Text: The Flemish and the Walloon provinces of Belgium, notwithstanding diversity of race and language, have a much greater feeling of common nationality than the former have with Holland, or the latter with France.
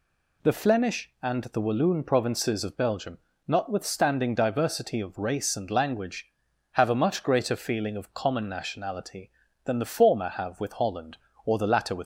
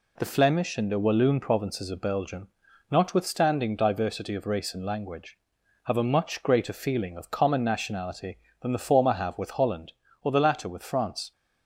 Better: second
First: stops before "France"; at 12.0 s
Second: none

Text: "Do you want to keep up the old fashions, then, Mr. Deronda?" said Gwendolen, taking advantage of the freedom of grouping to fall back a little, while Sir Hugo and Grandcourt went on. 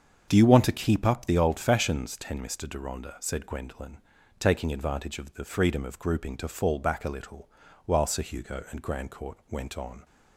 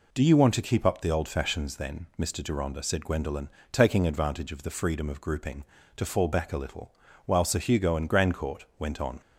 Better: second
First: starts louder than the rest; until 1.2 s; 7 dB // says "ten" for "then"; at 2.1 s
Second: none

